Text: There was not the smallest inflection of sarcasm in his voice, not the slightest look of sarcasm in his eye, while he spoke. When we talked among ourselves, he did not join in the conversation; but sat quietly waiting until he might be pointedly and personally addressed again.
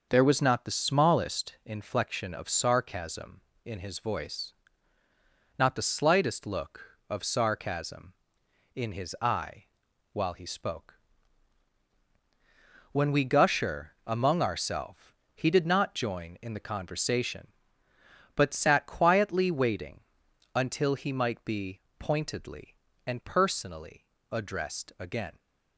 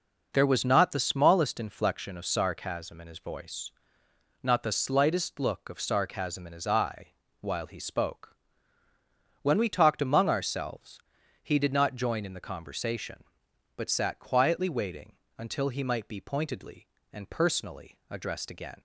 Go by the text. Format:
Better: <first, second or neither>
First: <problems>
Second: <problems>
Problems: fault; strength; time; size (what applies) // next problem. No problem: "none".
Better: second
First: starts louder than the rest; noticeable; until 1.1 s; 6 dB // says "gusher" for "talked"; at 13.2 s // pauses between "waiting" and "until"; noticeable; at 20.0 s; 0.54 s long // pauses between "be" and "pointedly"; slight; at 21.8 s; 0.18 s long // pauses between "personally" and "addressed"; slight; at 24.0 s; 0.24 s long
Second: pauses between "waiting" and "until"; slight; at 15.1 s; 0.20 s long